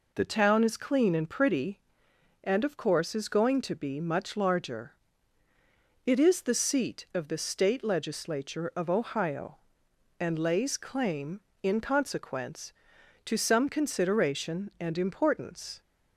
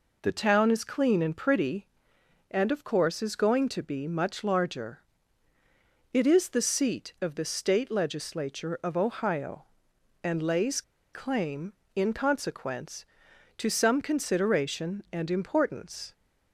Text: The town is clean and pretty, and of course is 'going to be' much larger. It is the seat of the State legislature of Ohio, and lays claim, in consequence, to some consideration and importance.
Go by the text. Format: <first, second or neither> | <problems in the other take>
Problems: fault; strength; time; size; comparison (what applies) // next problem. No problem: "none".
first | pauses between "lays" and "claim"; slight; at 10.8 s; 0.31 s long